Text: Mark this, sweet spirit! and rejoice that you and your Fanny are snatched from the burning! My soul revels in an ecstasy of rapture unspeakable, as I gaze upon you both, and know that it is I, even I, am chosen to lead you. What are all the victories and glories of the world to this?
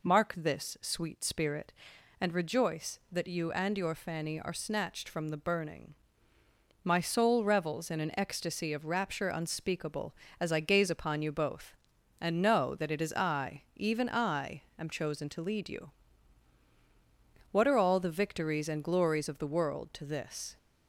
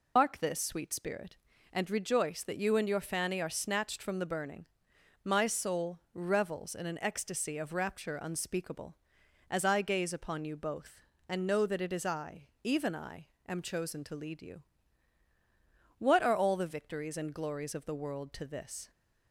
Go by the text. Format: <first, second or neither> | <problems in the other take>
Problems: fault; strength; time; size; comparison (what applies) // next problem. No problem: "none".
first | loses the start of "Mark"; at 0.1 s; 90 ms